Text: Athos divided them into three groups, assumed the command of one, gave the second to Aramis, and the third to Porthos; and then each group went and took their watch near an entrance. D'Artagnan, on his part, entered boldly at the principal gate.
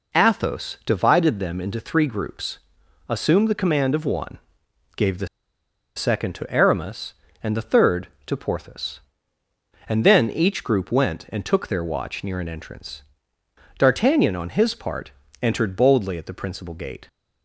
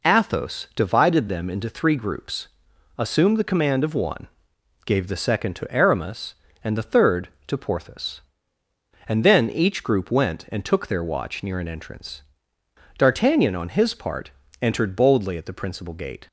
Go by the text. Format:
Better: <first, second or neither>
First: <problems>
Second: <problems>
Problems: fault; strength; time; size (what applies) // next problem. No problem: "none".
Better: second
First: pauses between "the" and "second"; noticeable; at 5.2 s; 0.69 s long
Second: none